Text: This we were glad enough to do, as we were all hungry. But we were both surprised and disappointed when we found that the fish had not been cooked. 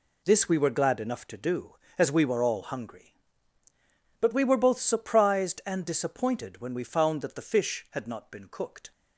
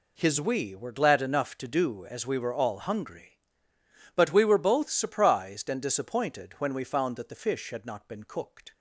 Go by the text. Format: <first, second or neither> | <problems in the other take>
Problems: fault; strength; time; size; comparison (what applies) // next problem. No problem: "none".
first | says "His" for "This"; at 0.1 s